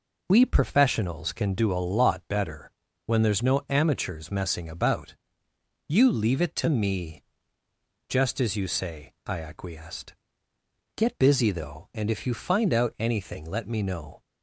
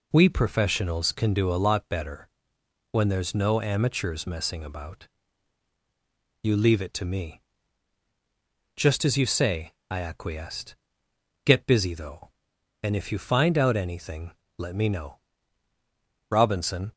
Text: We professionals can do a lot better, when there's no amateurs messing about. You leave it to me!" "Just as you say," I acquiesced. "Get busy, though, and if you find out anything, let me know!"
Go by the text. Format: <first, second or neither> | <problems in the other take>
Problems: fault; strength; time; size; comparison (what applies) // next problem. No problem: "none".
first | goes on to say "Robinson"; noticeable; from 16.2 s on; 0.62 s long